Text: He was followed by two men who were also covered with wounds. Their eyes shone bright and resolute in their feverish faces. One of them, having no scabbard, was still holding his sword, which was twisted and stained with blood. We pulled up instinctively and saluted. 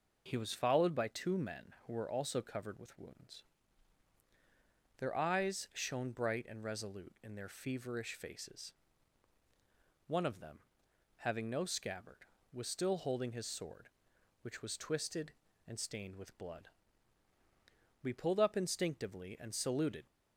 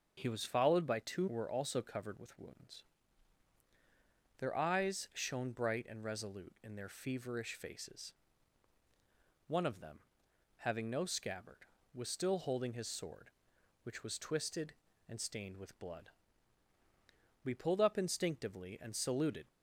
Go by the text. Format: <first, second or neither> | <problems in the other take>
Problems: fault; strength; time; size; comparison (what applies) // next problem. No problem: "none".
first | starts louder than the rest; until 1.1 s; 6.5 dB // skips "men"; at 1.2 s